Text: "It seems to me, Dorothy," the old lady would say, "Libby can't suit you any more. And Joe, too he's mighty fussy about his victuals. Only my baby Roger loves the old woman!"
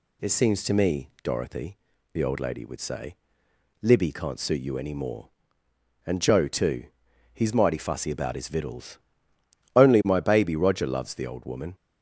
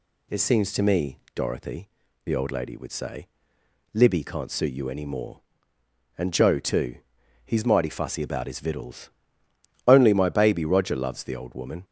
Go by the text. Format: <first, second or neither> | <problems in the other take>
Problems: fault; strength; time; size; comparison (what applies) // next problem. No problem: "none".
neither | pauses between "too" and "he's"; noticeable; the same in both